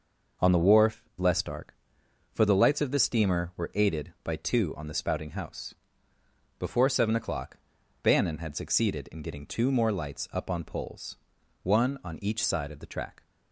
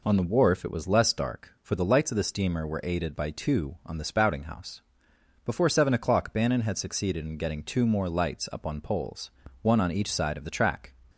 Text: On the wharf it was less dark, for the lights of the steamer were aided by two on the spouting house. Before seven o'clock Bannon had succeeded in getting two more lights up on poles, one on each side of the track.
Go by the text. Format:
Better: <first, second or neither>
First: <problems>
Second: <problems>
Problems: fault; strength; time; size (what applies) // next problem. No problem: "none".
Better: second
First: skips "it was"; at 1.1 s // pauses between "o'clock" and "Bannon"; at 7.5 s; 0.44 s long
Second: none